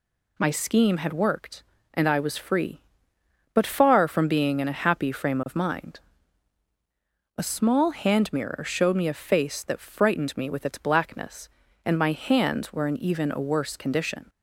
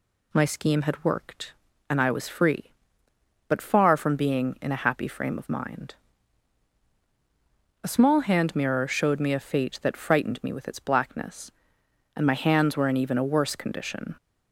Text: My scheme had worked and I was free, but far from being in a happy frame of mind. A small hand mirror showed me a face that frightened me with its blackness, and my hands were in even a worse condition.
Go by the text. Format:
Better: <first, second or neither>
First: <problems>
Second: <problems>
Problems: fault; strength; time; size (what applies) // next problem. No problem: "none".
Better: first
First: none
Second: says "fate" for "face"; at 9.3 s